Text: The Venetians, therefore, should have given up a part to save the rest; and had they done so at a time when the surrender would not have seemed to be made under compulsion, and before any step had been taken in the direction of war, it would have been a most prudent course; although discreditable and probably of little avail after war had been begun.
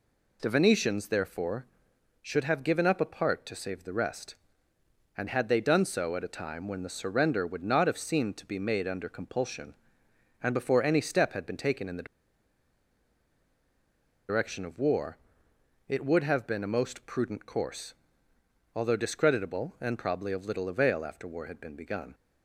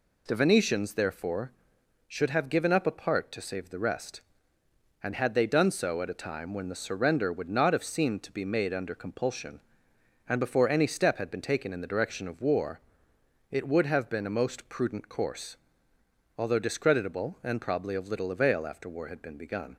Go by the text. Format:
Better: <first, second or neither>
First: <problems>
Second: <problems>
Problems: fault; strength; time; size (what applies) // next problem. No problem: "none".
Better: second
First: pauses between "the" and "direction"; strong; at 12.0 s; 2.2 s long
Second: none